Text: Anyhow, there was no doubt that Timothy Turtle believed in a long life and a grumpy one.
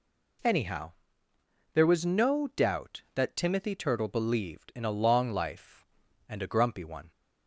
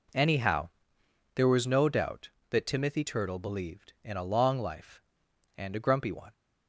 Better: neither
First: none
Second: none

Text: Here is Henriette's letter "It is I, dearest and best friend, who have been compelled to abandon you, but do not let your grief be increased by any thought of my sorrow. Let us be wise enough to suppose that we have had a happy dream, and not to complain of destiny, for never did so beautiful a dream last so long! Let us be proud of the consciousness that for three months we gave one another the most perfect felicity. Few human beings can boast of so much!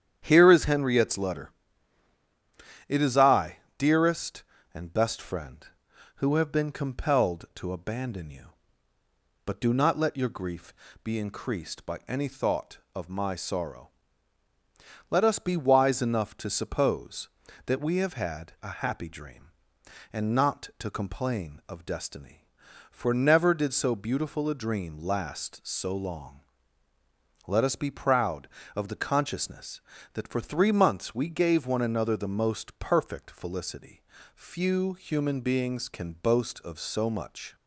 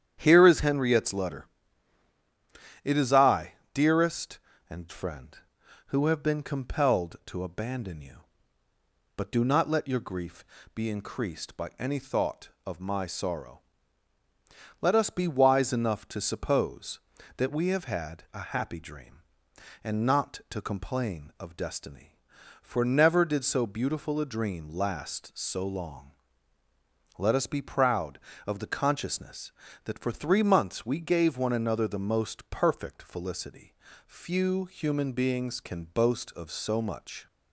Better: first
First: starts louder than the rest; strong; until 1.2 s; 9 dB // pauses between "letter" and "It"; strong; at 1.4 s; 1.3 s long // pauses between "grief" and "be"; slight; at 10.7 s; 0.32 s long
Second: starts louder than the rest; strong; until 1.2 s; 9 dB // pauses between "letter" and "It"; strong; at 1.4 s; 1.3 s long // skips "best"; at 4.8 s // pauses between "grief" and "be"; slight; at 10.4 s; 0.32 s long

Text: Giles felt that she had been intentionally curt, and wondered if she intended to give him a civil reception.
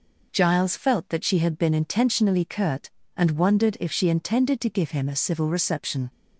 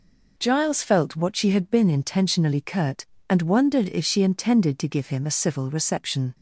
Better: first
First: none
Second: says "what" for "that"; at 1.1 s

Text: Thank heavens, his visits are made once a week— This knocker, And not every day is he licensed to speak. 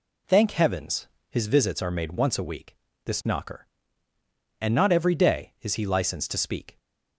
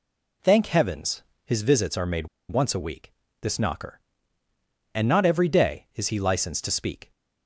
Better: first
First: none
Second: pauses between "made" and "once"; slight; at 2.2 s; 0.21 s long

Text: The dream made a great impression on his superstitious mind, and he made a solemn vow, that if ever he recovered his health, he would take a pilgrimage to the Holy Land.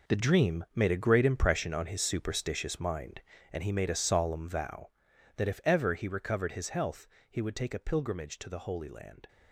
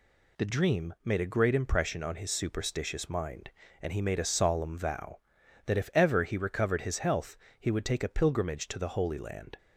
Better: second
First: gets quieter; strong; throughout; 12.5 dB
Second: none

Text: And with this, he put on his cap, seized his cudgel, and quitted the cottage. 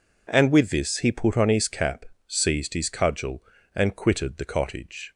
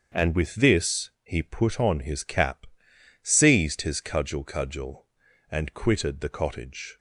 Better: first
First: none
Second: starts louder than the rest; until 1.2 s; 7 dB // says "cudgel" twice; at 4.4 s

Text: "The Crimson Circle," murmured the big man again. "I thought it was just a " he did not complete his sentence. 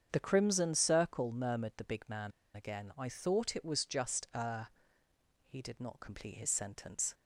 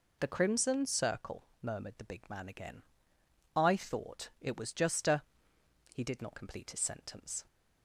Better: second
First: starts louder than the rest; strong; until 1.1 s; 8 dB // pauses between "man" and "again"; slight; at 2.3 s; 0.24 s long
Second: none

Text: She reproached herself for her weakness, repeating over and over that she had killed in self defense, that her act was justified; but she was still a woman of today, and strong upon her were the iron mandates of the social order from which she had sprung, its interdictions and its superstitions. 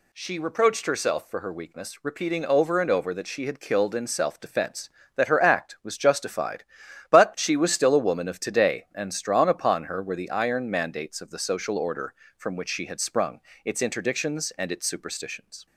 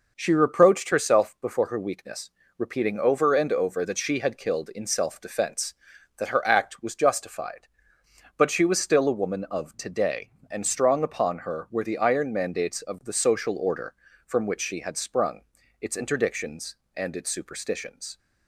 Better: first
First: none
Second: says "before" for "for"; at 1.4 s

